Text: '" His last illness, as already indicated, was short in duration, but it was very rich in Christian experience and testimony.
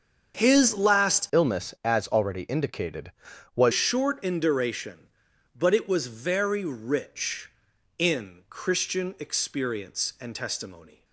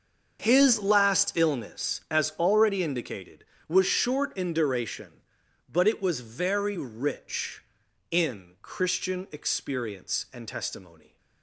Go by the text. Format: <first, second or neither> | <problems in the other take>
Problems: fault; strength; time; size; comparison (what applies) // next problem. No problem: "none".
second | starts louder than the rest; until 1.4 s; 7 dB; also in the second // changes voice from "illness" to "was"; from 1.3 to 3.7 s; 2.4 s long